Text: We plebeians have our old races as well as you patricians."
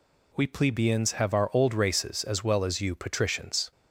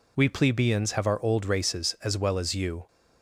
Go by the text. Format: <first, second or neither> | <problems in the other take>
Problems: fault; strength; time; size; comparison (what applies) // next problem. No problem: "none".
first | stops before "patricians"; at 2.8 s